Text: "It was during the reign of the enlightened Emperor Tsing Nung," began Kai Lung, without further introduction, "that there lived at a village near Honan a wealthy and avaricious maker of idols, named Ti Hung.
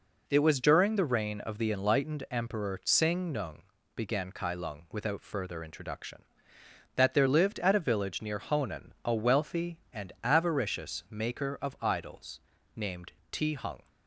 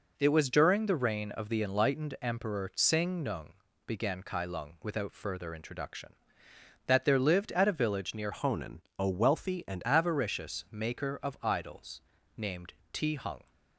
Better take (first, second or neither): first